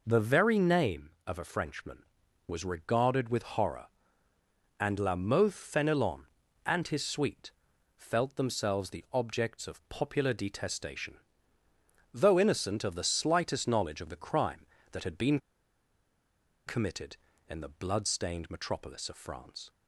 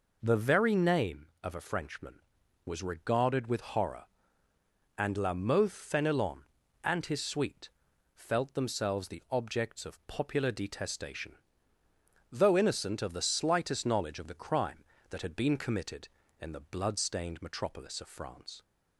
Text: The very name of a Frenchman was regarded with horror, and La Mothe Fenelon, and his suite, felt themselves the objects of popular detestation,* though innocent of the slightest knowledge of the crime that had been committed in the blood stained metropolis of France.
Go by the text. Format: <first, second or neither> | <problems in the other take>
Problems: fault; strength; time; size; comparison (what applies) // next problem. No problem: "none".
second | pauses between "been" and "committed"; strong; at 15.3 s; 1.2 s long